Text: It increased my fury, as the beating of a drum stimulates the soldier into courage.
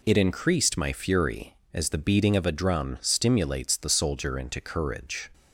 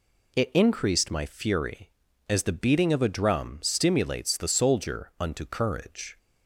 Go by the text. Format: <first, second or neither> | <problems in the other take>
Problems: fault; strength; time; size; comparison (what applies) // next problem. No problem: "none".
first | says "unto" for "into"; at 5.1 s